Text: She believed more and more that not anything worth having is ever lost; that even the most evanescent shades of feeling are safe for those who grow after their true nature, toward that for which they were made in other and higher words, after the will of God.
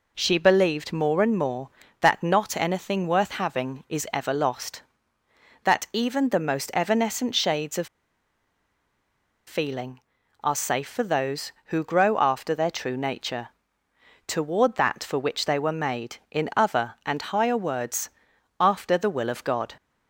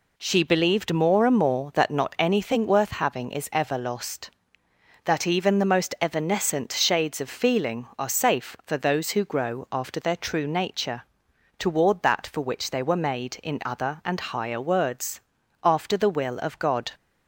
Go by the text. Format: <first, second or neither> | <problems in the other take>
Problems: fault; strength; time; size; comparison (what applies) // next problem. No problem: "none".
second | pauses between "of" and "feeling"; strong; at 7.8 s; 1.6 s long